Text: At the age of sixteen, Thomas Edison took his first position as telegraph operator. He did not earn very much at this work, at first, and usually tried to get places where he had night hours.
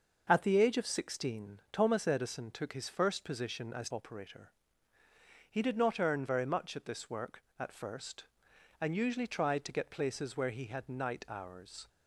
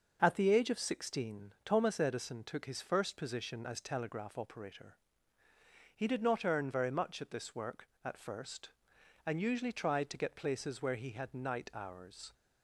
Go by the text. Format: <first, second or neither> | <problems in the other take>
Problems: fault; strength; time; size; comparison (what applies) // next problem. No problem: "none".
second | skips "telegraph"; at 3.8 s